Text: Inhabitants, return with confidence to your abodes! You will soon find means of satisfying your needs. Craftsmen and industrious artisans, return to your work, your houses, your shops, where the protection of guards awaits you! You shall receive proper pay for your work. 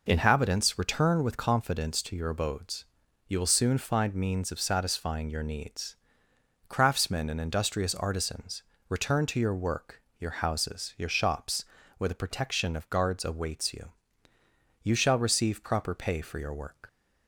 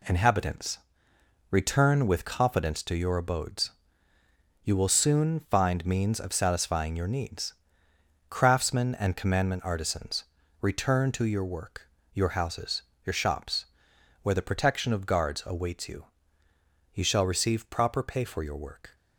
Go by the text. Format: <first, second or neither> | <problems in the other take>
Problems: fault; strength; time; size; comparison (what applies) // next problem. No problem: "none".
first | says "commandment" for "industrious"; at 9.1 s